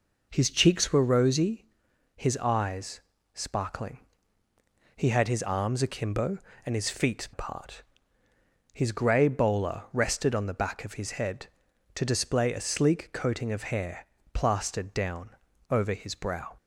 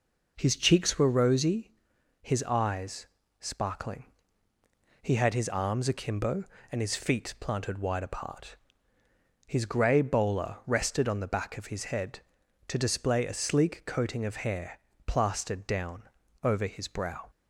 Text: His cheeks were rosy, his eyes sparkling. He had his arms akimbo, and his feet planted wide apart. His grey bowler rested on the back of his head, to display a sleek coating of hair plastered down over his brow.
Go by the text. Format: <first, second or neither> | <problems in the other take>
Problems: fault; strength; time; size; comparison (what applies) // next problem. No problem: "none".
second | pauses between "eyes" and "sparkling"; slight; at 3.0 s; 0.32 s long; slight in the second // skips "planted wide"; at 7.3 s // pauses between "hair" and "plastered"; slight; at 14.0 s; 0.26 s long; slight in the second // pauses between "down" and "over"; at 15.2 s; 0.40 s long; also in the second